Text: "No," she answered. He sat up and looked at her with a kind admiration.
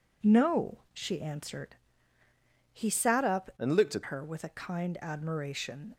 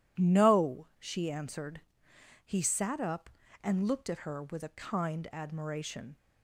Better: second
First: changes voice from "and" to "at"; from 3.5 to 4.0 s; 0.5 s long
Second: none

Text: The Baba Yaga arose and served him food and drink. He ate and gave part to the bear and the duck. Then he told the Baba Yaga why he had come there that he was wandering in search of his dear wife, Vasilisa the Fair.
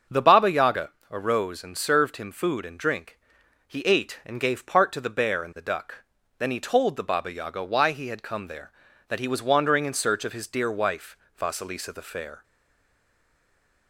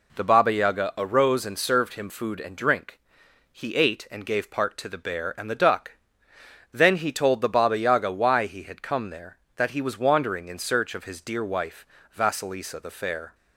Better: second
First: starts louder than the rest; until 1.3 s; 7 dB // pauses between "Yaga" and "arose"; slight; at 0.9 s; 0.20 s long // stays silent after the last word; noticeable; from 12.4 s on; 1.4 s long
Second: none

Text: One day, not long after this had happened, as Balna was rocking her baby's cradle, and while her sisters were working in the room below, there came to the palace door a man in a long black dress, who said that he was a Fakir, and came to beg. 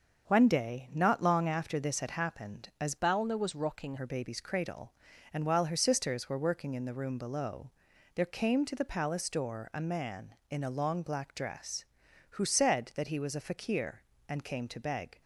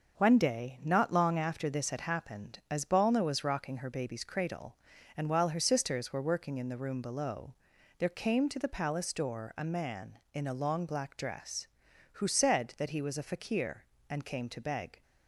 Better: second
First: starts louder than the rest; until 1.3 s; 6.5 dB // changes voice from "Balna" to "rocking"; from 2.9 to 3.9 s; 1.0 s long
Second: starts louder than the rest; until 1.2 s; 6.5 dB

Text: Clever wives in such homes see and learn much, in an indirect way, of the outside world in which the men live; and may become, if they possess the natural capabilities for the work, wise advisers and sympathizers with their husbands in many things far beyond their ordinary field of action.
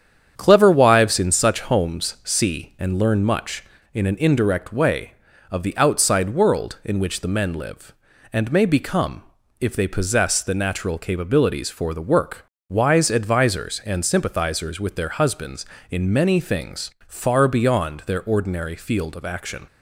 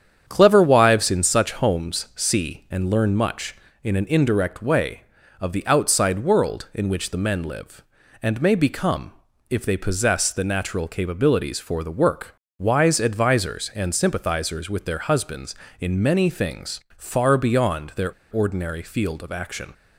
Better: first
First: starts louder than the rest; strong; until 1.3 s; 8.5 dB // pauses between "things" and "far"; slight; at 16.9 s; 0.16 s long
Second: starts louder than the rest; strong; until 1.2 s; 8.5 dB // pauses between "things" and "far"; slight; at 16.8 s; 0.16 s long // pauses between "their" and "ordinary"; slight; at 18.1 s; 0.20 s long

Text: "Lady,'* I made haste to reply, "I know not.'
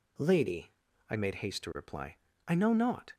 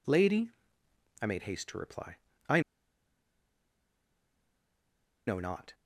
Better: first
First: none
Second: pauses between "I" and "know"; strong; at 2.6 s; 2.6 s long

